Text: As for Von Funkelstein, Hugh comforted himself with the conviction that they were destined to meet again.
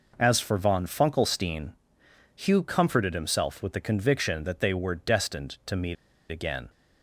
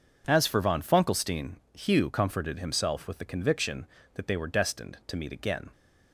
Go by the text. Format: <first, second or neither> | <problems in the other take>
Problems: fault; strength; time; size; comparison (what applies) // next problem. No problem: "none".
second | pauses between "meet" and "again"; slight; at 5.9 s; 0.35 s long